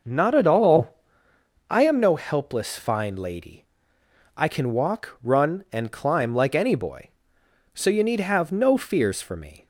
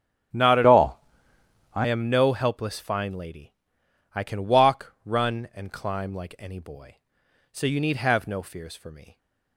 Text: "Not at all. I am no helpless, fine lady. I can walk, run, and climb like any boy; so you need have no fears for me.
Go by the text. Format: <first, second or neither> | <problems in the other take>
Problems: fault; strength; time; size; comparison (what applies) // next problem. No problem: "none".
first | starts louder than the rest; strong; until 2.1 s; 11 dB // changes voice from "all" to "I"; from 0.6 to 1.8 s; 1.2 s long